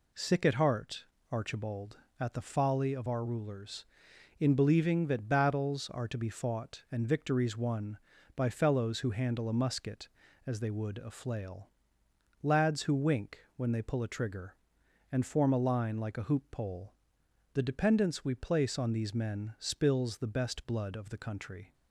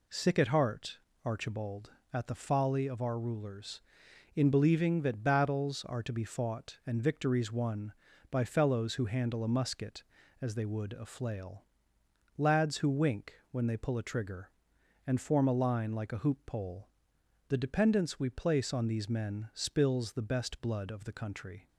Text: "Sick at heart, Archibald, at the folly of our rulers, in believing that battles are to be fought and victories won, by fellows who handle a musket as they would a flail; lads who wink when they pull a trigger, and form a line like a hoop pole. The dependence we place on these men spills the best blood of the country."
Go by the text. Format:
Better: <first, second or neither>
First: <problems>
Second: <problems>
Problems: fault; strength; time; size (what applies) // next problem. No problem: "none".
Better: neither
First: none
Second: none